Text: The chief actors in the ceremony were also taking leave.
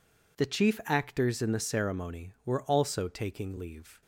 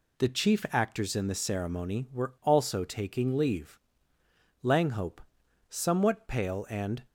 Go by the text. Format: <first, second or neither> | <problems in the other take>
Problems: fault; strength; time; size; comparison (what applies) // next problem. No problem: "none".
first | goes on to say "Langhope somewhat pale and"; strong; from 4.6 s on; 2.4 s long